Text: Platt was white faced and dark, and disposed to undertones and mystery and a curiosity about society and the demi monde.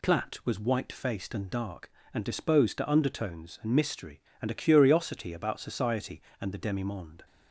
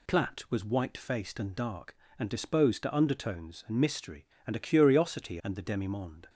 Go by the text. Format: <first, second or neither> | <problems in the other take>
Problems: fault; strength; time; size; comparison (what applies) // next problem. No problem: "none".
first | skips "about society"; at 5.4 s